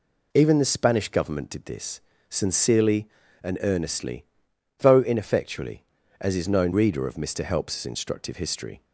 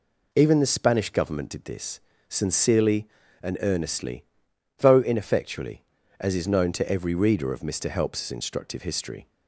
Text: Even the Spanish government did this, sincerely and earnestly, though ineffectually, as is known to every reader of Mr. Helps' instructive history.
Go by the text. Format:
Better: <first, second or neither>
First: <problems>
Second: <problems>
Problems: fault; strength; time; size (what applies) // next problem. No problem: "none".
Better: second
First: skips "to every"; at 6.7 s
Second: none